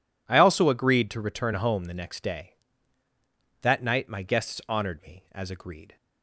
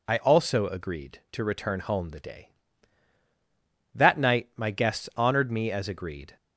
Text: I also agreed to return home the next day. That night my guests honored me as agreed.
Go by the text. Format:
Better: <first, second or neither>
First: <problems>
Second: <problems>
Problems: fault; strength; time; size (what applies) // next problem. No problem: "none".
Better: first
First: none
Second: skips "next"; at 2.1 s